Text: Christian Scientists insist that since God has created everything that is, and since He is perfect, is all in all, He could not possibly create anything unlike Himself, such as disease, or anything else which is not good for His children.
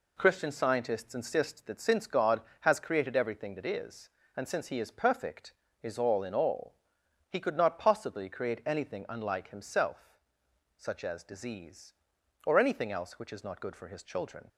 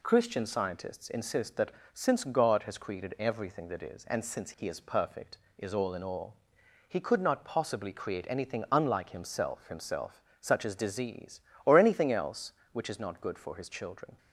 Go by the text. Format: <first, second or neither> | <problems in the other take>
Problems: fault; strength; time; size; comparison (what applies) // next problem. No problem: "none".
first | pauses between "that" and "since"; slight; at 1.7 s; 0.22 s long // says "Himself" twice; at 9.6 s